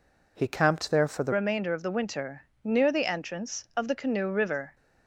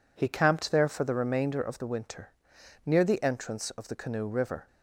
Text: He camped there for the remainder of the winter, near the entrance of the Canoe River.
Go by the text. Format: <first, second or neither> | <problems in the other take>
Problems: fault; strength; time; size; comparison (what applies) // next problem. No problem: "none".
second | changes voice at "remainder"; from 1.3 s on; 3.4 s long